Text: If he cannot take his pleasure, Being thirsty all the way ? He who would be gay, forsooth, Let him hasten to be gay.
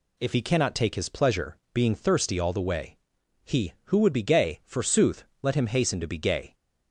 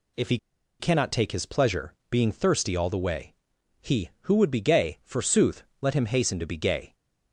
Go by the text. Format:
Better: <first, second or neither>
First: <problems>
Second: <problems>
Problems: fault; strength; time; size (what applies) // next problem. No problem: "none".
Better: first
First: none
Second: pauses between "he" and "cannot"; at 0.3 s; 0.42 s long